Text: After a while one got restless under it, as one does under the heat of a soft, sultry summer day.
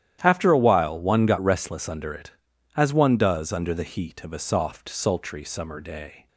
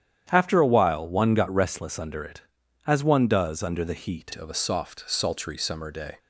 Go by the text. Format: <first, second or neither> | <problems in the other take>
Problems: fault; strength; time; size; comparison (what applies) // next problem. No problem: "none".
first | starts louder than the rest; strong; until 1.3 s; 10 dB; strong in the first // changes voice at "of"; from 4.3 s on; 1.8 s long